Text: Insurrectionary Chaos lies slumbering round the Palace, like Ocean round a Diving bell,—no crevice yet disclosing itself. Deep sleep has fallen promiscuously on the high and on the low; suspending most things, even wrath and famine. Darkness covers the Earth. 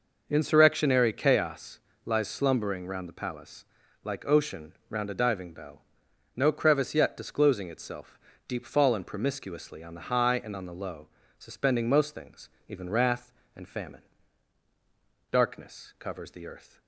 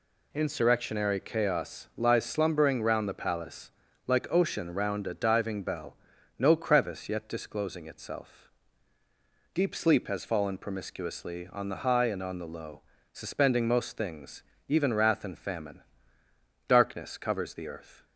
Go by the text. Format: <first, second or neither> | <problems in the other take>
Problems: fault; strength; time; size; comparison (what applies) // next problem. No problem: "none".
second | pauses between "Chaos" and "lies"; slight; at 1.7 s; 0.26 s long // pauses between "Ocean" and "round"; slight; at 4.7 s; 0.18 s long // skips "sleep has"; at 8.6 s